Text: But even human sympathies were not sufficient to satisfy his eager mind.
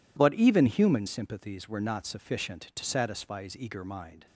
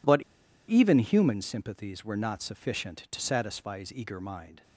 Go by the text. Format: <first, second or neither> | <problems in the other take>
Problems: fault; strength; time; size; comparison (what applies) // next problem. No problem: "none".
first | pauses between "But" and "even"; noticeable; at 0.2 s; 0.47 s long